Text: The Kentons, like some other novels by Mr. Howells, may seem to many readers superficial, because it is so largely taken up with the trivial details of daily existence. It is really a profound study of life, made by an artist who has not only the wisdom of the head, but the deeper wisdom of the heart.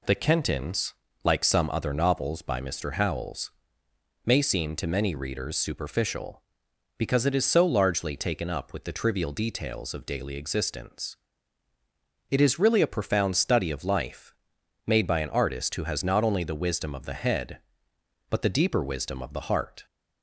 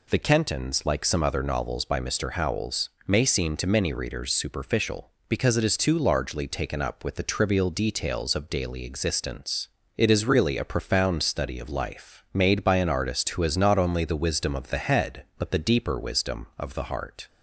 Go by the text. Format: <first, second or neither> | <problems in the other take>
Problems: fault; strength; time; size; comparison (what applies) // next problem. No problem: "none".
first | says "too" for "so"; at 5.7 s